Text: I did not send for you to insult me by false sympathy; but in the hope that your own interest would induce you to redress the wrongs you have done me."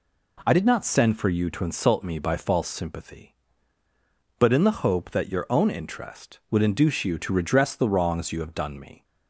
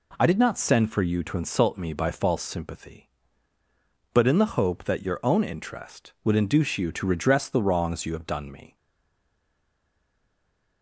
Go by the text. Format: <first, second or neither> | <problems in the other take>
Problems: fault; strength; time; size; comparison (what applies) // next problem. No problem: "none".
first | stays silent after the last word; from 8.7 s on; 2.1 s long